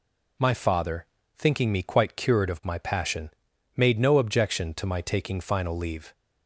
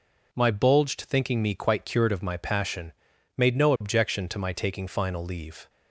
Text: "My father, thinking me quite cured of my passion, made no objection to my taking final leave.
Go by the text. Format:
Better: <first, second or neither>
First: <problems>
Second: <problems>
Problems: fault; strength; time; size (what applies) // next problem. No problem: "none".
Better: first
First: none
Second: says "bulged" for "father"; at 0.4 s